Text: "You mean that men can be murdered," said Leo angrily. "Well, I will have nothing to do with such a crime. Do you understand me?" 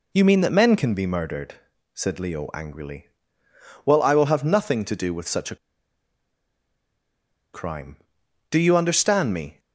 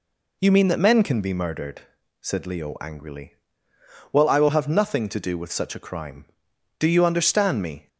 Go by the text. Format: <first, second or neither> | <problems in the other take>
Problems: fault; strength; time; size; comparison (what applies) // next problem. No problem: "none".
second | pauses between "a" and "crime"; strong; at 5.5 s; 1.9 s long